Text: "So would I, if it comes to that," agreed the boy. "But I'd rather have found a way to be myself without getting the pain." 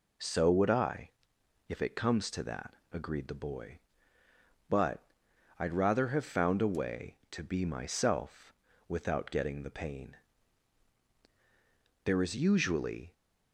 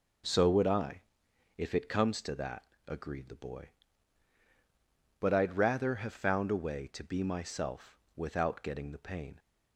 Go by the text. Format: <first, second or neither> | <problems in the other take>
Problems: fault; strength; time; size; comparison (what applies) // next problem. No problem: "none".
second | pauses between "But" and "I'd"; noticeable; at 5.0 s; 0.56 s long // pauses between "myself" and "without"; slight; at 8.5 s; 0.34 s long; slight in the second // goes on to say "There is usually"; noticeable; from 12.0 s on; 1.0 s long